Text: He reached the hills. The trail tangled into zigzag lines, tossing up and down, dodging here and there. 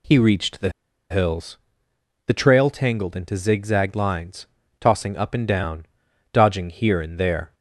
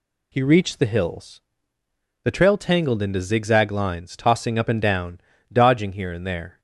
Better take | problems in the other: second | pauses between "the" and "hills"; at 0.6 s; 0.40 s long

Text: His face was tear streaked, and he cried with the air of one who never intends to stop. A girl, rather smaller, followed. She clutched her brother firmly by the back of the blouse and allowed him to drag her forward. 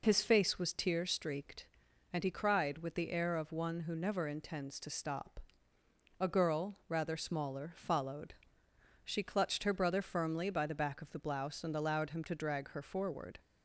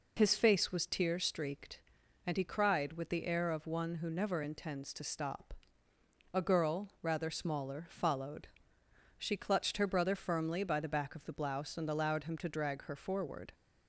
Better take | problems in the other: neither | none

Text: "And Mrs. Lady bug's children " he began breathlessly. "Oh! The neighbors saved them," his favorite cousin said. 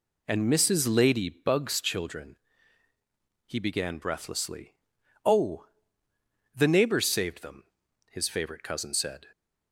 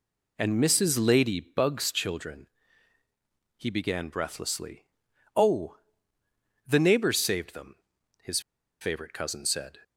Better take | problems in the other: first | pauses between "his" and "favorite"; at 8.3 s; 0.41 s long

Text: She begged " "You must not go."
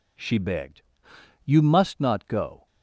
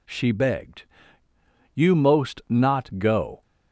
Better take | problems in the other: first | says "most" for "must"; at 1.9 s

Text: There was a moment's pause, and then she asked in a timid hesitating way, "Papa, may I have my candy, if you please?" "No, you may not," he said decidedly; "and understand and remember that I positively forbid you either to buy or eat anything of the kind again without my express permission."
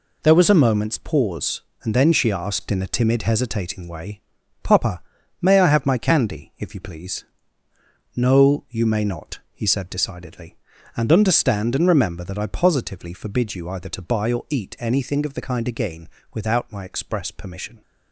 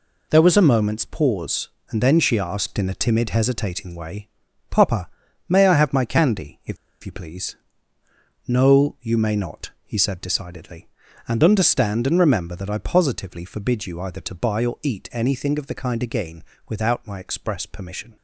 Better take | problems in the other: first | pauses between "if" and "you"; slight; at 6.7 s; 0.27 s long // pauses between "again" and "without"; slight; at 16.4 s; 0.24 s long; slight in the first

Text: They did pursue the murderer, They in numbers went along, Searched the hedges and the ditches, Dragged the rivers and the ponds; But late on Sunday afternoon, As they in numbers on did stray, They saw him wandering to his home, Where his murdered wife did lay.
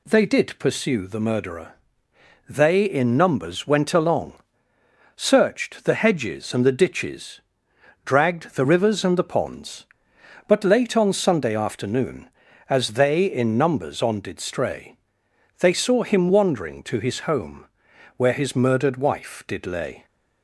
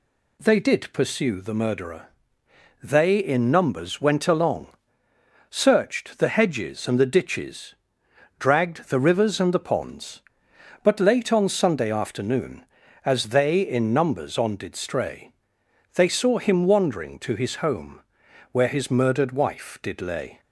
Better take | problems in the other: neither | none

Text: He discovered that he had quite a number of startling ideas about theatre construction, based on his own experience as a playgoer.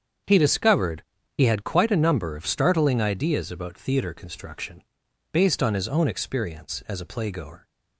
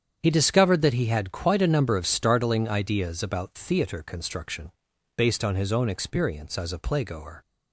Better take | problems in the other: second | starts louder than the rest; strong; until 1.6 s; 7.5 dB; strong in the second // skips "that"; at 1.1 s

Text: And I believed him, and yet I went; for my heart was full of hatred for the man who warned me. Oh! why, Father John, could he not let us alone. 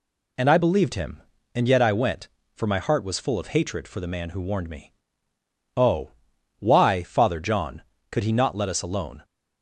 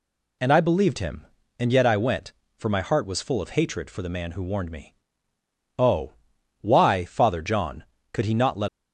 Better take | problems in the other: first | stops before "us alone"; at 8.6 s

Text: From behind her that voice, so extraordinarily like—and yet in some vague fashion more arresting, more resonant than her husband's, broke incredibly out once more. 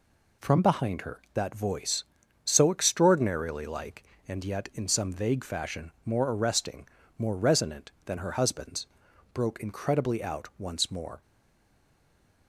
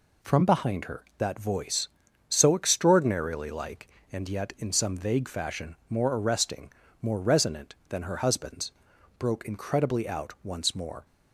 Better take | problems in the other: second | stays silent after the last word; noticeable; from 11.2 s on; 1.2 s long

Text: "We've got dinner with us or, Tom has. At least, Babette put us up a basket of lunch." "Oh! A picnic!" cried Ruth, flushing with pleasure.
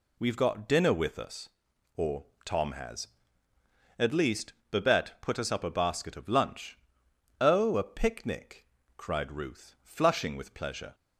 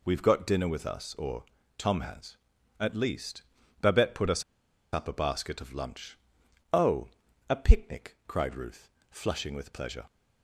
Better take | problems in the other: first | pauses between "us" and "up"; noticeable; at 4.4 s; 0.50 s long

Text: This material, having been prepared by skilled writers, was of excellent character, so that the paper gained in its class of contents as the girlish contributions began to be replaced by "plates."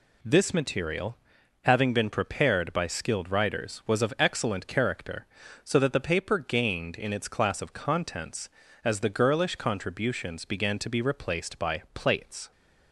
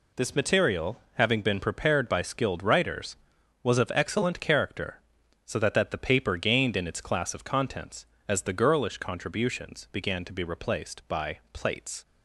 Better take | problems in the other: first | says "that" twice; at 5.7 s

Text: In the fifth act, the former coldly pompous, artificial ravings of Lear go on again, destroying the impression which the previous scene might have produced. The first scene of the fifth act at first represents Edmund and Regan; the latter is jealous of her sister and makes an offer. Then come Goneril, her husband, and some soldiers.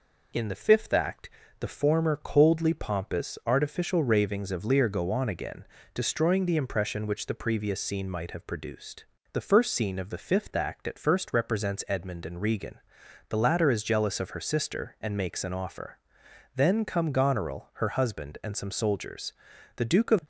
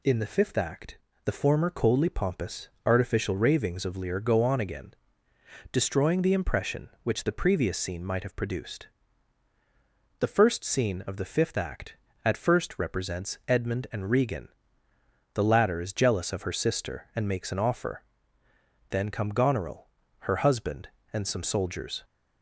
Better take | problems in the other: second | goes on to say "The Duke of"; slight; from 19.7 s on; 0.44 s long

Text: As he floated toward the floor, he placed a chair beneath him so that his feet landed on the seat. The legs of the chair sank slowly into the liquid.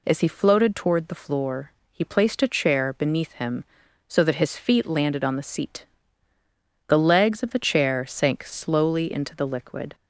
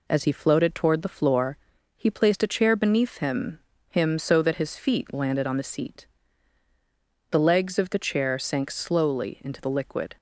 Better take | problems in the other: first | says "him" twice; at 3.8 s

